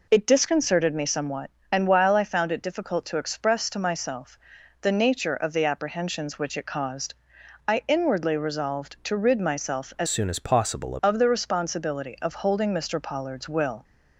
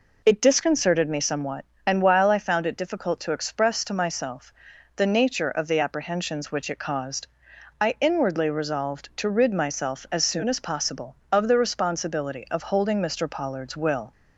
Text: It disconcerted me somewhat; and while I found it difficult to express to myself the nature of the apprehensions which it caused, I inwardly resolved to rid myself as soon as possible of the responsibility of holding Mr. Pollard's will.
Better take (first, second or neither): second